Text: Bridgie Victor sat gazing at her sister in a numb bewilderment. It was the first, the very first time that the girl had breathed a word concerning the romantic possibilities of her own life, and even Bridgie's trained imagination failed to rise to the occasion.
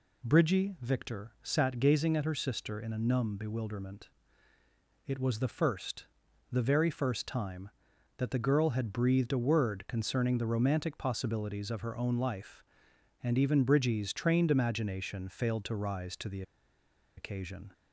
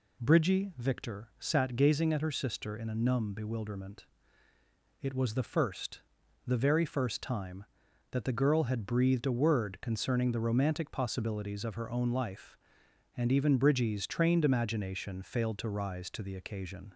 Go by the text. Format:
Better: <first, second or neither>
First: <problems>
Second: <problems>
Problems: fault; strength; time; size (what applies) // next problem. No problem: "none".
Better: second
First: pauses between "the" and "occasion"; noticeable; at 16.4 s; 0.75 s long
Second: none